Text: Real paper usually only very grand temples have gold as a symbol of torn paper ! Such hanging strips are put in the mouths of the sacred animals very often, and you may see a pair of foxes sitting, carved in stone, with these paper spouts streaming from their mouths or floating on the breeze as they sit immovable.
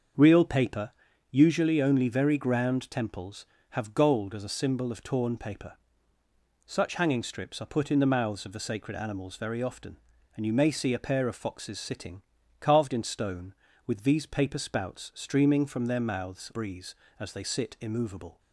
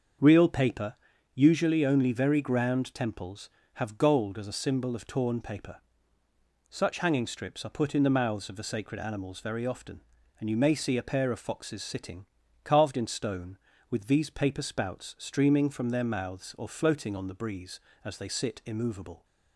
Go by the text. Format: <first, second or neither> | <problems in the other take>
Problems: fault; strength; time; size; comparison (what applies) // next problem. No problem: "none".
second | starts louder than the rest; until 1.5 s; 6.5 dB; also in the second // pauses between "paper" and "usually"; at 0.9 s; 0.38 s long; also in the second // skips "or floating on the"; at 16.5 s